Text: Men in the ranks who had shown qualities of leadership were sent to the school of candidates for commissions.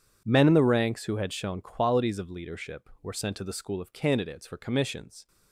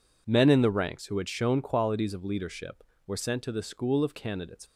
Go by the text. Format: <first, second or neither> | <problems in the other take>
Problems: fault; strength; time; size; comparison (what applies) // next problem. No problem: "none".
first | stops before "for commissions"; at 4.6 s